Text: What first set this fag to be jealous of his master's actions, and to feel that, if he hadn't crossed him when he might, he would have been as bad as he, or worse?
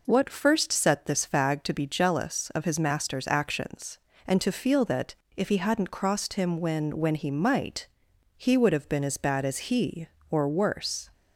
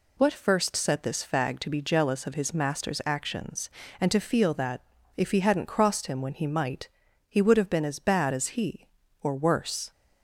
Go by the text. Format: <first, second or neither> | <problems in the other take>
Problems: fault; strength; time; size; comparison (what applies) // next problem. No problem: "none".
second | says "when" twice; at 6.9 s